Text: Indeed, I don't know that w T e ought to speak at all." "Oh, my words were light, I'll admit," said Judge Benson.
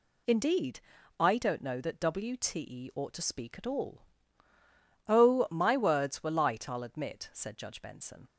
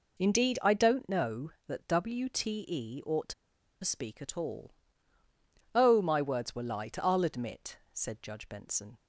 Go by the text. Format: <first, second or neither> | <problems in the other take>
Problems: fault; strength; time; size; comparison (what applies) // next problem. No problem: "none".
first | pauses between "to" and "speak"; noticeable; at 3.3 s; 0.50 s long